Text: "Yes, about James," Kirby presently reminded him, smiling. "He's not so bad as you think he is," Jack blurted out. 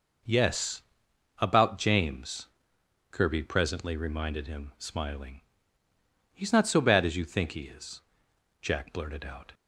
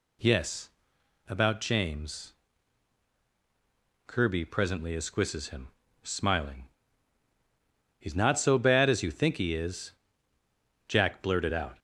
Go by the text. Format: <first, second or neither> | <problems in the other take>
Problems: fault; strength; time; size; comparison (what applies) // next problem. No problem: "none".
first | says "esquisses" for "reminded"; at 4.9 s